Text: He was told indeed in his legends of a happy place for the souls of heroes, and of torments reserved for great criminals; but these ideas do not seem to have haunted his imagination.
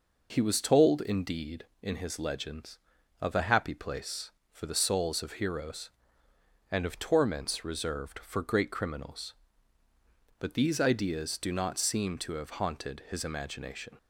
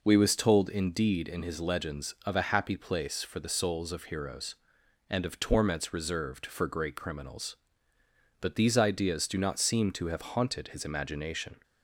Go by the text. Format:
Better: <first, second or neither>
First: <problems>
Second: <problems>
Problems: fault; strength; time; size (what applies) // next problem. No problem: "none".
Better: first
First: none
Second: says "We" for "He"; at 0.0 s